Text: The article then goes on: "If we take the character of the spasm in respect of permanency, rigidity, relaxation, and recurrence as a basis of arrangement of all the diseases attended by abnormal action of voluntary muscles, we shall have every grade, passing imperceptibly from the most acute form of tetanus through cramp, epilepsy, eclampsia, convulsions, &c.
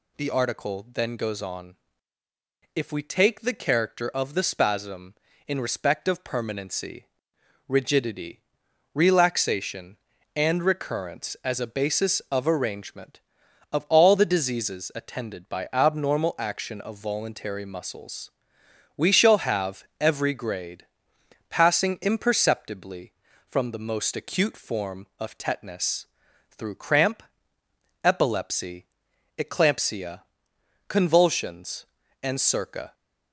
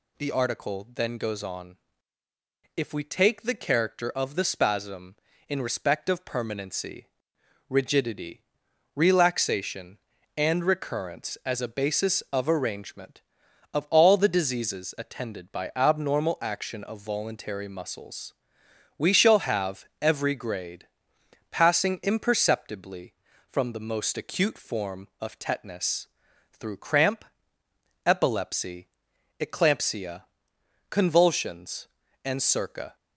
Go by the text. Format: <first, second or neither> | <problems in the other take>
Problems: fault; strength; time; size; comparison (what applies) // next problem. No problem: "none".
neither | pauses between "tetanus" and "through"; the same in both